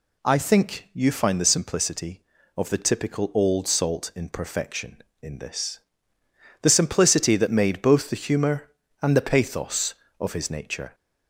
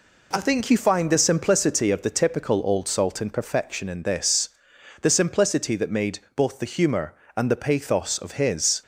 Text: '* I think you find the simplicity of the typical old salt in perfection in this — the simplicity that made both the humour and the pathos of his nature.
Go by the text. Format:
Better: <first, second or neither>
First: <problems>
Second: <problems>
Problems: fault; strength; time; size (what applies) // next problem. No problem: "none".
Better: first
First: none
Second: pauses between "made" and "both"; slight; at 6.1 s; 0.16 s long // stops before "nature"; at 8.8 s